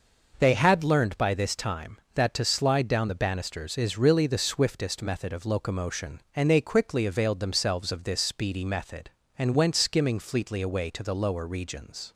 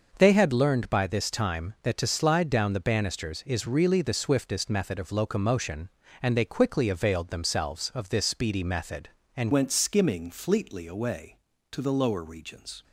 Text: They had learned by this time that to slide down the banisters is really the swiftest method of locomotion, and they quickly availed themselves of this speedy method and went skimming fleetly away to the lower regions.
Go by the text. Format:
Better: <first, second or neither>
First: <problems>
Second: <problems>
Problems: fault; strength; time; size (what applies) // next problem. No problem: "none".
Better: first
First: none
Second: changes voice at "went"; from 9.5 s on; 3.3 s long